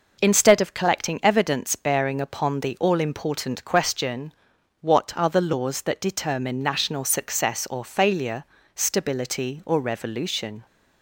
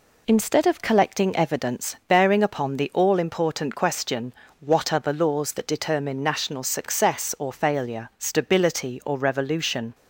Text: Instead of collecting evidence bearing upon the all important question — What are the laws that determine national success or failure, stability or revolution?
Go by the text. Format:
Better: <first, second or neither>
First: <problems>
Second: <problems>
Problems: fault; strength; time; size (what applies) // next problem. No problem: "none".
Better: neither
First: none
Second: none